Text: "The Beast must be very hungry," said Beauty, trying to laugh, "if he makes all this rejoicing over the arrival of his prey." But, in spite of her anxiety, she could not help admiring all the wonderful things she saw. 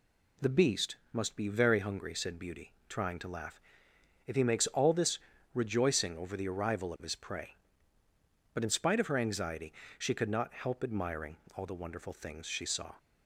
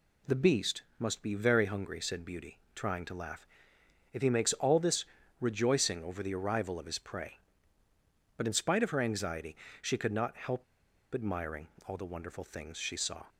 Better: first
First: pauses between "this" and "rejoicing"; slight; at 5.1 s; 0.34 s long // pauses between "admiring" and "all"; slight; at 11.3 s; 0.20 s long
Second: pauses between "this" and "rejoicing"; slight; at 5.0 s; 0.34 s long // pauses between "help" and "admiring"; noticeable; at 10.6 s; 0.49 s long // pauses between "admiring" and "all"; slight; at 11.6 s; 0.20 s long

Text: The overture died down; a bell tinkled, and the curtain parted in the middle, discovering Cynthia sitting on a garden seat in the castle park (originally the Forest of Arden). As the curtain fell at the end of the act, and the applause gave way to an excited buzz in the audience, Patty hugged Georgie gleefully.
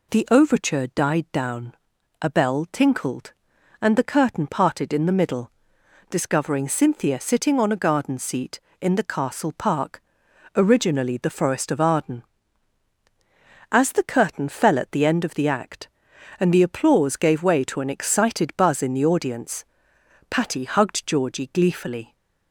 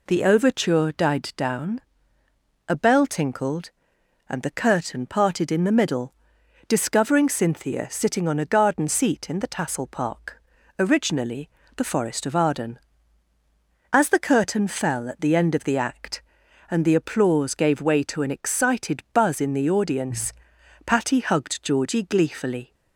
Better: first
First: none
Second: says "tassel" for "castle"; at 9.4 s // pauses between "originally" and "the"; slight; at 11.4 s; 0.26 s long

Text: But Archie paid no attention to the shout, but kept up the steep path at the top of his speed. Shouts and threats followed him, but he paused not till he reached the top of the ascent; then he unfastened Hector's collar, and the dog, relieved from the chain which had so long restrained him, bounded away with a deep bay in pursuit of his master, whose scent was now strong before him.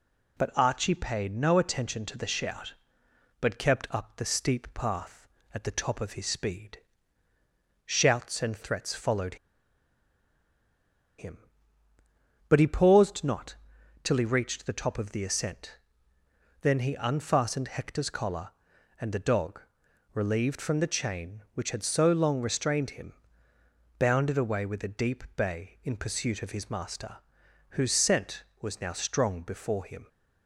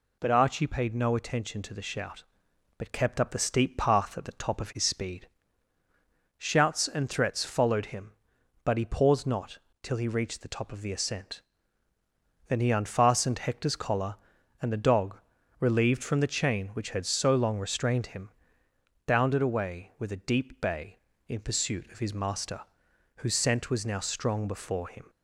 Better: second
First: pauses between "followed" and "him"; strong; at 9.3 s; 1.8 s long // pauses between "not" and "till"; noticeable; at 13.5 s; 0.48 s long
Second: pauses between "not" and "till"; slight; at 9.5 s; 0.24 s long

